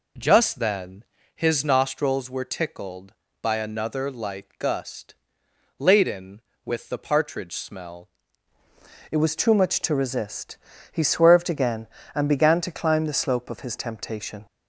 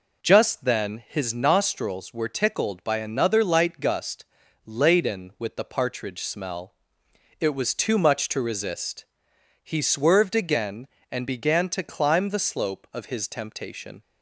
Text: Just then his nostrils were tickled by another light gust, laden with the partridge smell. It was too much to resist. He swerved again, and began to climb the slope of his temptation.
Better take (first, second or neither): second